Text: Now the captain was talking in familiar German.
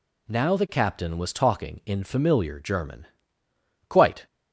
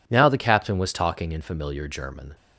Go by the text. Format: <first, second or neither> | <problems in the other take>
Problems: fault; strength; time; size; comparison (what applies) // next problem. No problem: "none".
second | goes on to say "Quite"; slight; from 3.8 s on; 0.38 s long